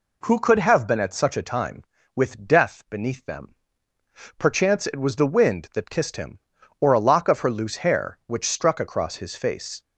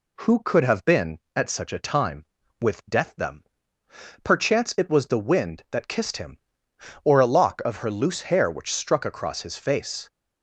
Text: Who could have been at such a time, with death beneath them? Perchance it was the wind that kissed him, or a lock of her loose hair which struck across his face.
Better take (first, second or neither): first